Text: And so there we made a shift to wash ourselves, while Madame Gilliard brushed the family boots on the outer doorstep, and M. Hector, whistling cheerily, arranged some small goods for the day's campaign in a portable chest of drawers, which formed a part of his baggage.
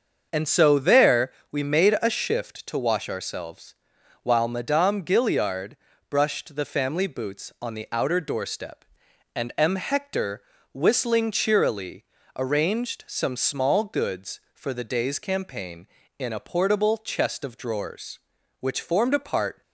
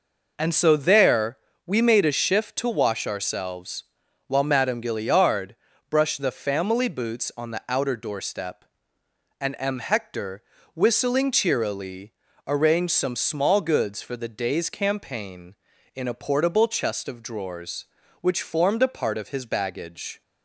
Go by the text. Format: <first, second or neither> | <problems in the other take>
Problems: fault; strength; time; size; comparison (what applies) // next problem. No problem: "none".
second | starts louder than the rest; until 1.3 s; 6.5 dB // pauses between "there" and "we"; slight; at 1.3 s; 0.18 s long; slight in the second // pauses between "Gilliard" and "brushed"; slight; at 5.7 s; 0.36 s long; slight in the second // stops before "of his baggage"; at 19.6 s